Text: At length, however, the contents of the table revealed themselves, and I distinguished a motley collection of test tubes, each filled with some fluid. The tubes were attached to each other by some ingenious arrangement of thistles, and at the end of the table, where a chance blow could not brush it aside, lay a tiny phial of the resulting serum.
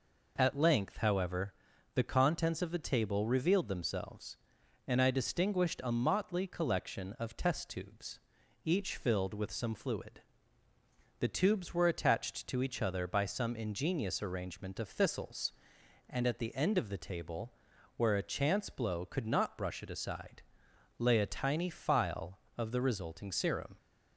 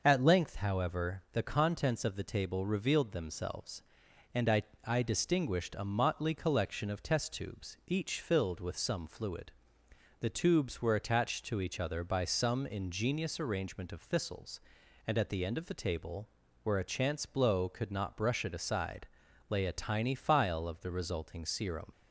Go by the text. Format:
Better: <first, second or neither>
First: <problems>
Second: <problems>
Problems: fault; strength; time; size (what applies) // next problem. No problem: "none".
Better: first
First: none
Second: says "I" twice; at 4.8 s